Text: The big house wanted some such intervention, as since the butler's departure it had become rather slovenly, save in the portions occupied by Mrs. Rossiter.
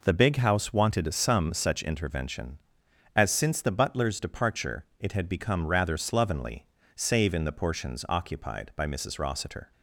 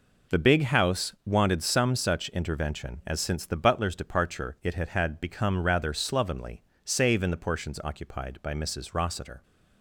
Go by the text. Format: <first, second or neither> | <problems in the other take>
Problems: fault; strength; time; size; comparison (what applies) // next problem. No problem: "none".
first | says "had" twice; at 4.8 s